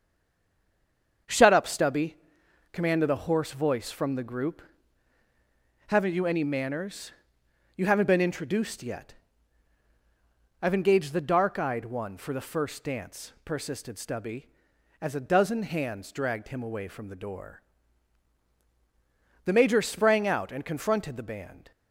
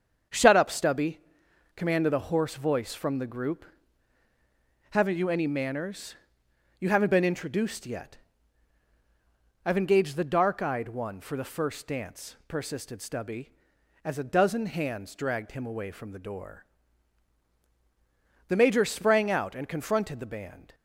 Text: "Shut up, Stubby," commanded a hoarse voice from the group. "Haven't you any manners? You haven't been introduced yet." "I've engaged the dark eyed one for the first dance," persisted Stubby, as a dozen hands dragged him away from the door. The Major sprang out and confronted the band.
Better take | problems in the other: second | stays silent before the first word; noticeable; until 1.2 s; 1.2 s long // starts louder than the rest; strong; until 2.8 s; 7 dB; strong in the second

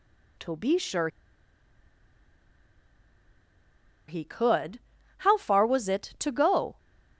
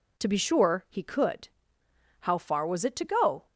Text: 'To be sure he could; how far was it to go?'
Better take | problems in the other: second | pauses between "sure" and "he"; strong; at 1.0 s; 3.0 s long

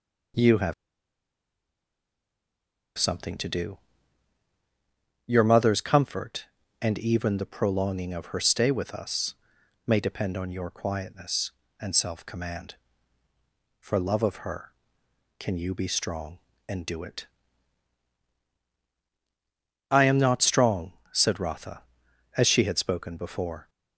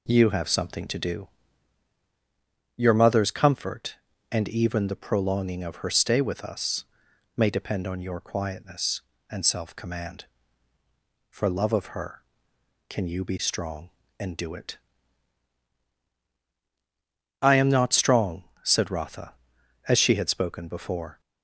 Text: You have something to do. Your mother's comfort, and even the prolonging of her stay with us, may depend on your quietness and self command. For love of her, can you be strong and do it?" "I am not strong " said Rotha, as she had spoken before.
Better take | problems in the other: second | pauses between "have" and "something"; strong; at 0.7 s; 2.2 s long

